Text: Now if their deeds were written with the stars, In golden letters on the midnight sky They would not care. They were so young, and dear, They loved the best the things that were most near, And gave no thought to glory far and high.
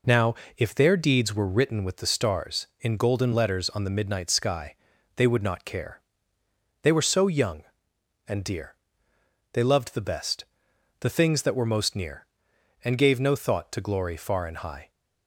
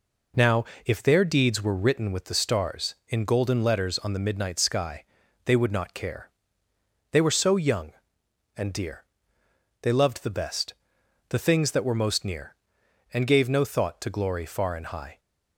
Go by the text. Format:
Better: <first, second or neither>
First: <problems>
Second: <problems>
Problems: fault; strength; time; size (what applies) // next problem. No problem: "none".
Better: neither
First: pauses between "Now" and "if"; slight; at 0.3 s; 0.22 s long // pauses between "sky" and "They"; at 4.7 s; 0.40 s long // pauses between "best" and "the"; noticeable; at 10.4 s; 0.56 s long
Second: pauses between "Now" and "if"; slight; at 0.6 s; 0.20 s long // pauses between "sky" and "They"; at 5.0 s; 0.40 s long // pauses between "best" and "the"; noticeable; at 10.7 s; 0.56 s long